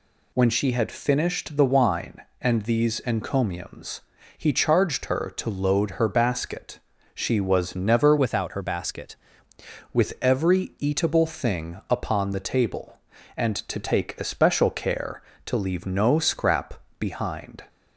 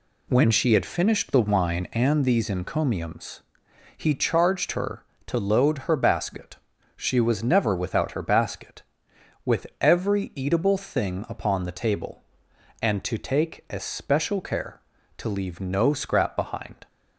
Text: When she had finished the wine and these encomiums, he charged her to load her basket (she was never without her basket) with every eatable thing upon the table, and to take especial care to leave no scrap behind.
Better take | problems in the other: second | changes voice from "without" to "basket"; from 8.1 to 9.1 s; 1.0 s long // pauses between "scrap" and "behind"; slight; at 16.8 s; 0.18 s long

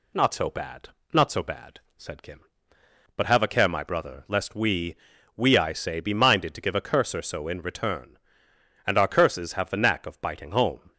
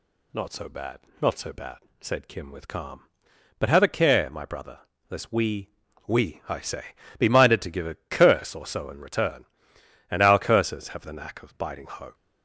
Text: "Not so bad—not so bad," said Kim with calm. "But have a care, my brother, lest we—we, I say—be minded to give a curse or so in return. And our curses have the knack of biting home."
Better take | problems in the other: second | skips "with calm"; at 2.7 s

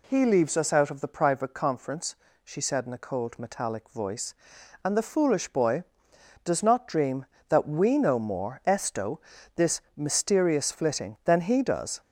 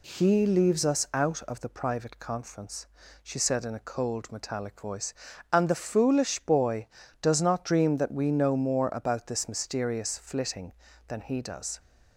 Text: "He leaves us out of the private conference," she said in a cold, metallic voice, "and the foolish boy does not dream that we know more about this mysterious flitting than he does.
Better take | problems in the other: second | says "esto" for "about"; at 8.6 s // pauses between "this" and "mysterious"; slight; at 9.8 s; 0.16 s long

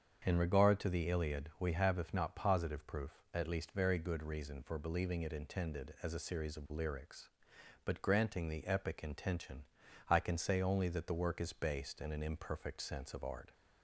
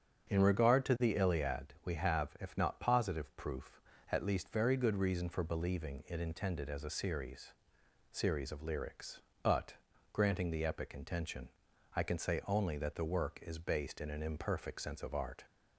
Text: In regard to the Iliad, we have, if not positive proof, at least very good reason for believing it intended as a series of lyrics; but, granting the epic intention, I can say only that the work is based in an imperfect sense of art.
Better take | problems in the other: first | starts louder than the rest; strong; until 1.3 s; 7.5 dB; strong in the first // says "series" twice; at 8.1 s

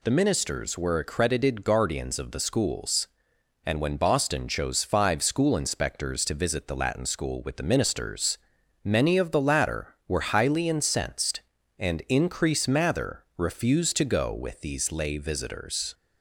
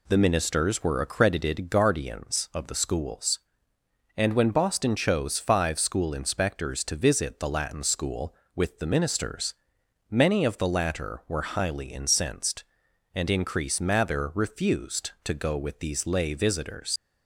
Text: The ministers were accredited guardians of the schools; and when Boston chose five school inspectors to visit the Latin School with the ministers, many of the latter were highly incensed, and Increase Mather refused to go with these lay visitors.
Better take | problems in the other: first | leaves "visitors" unfinished; at 16.9 s; 65 ms

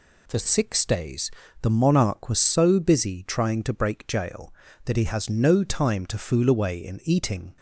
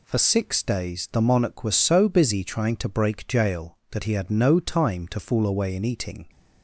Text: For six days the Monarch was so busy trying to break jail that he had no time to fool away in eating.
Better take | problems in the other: second | pauses between "days" and "the"; slight; at 1.3 s; 0.30 s long // says "has" for "had"; at 5.0 s

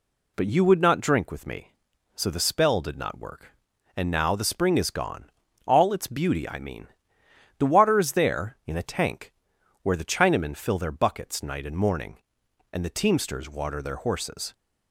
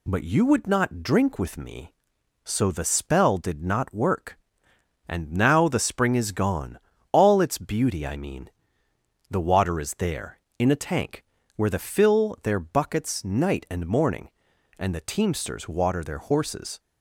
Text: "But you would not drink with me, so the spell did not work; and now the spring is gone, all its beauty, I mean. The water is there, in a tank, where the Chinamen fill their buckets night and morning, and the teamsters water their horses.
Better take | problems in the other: first | skips "Chinamen"; at 11.7 s

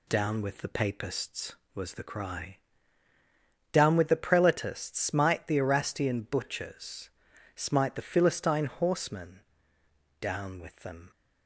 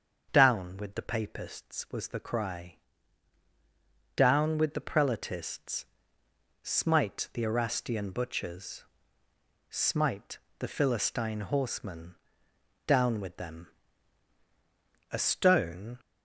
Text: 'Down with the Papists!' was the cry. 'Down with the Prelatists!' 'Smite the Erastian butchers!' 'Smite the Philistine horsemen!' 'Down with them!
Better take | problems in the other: first | starts louder than the rest; until 1.3 s; 6.5 dB // pauses between "Smite" and "the"; slight; at 10.3 s; 0.22 s long // goes on to say "A stone"; noticeable; from 15.0 s on; 0.90 s long

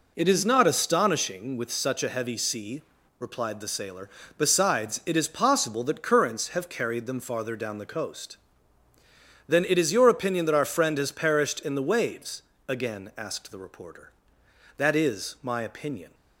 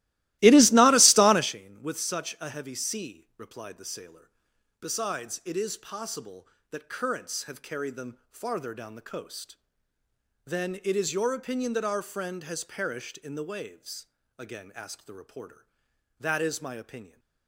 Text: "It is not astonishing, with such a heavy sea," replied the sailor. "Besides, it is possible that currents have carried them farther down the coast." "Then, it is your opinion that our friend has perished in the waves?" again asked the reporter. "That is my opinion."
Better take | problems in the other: first | starts louder than the rest; strong; until 1.6 s; 18 dB

